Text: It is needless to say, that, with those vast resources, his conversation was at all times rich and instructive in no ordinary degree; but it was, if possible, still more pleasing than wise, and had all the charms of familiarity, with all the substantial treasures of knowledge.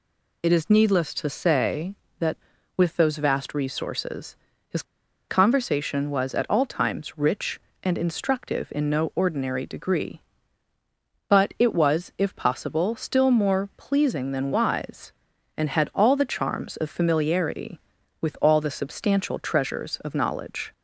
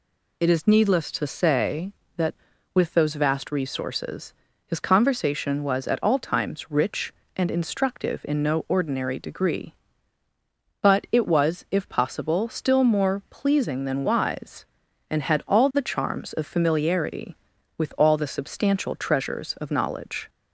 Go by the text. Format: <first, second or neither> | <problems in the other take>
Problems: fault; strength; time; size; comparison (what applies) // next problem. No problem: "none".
second | pauses between "his" and "conversation"; at 4.8 s; 0.45 s long